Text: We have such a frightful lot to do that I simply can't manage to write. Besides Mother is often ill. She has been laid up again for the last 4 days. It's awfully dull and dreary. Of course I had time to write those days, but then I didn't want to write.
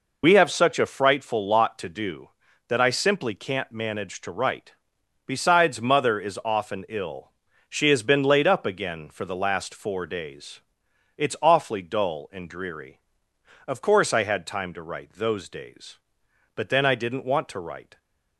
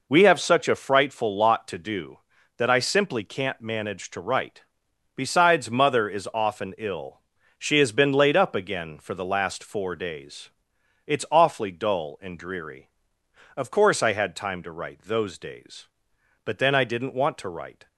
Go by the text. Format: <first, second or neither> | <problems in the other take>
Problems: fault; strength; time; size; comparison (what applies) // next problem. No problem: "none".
second | loses the start of "We"; at 0.2 s; 35 ms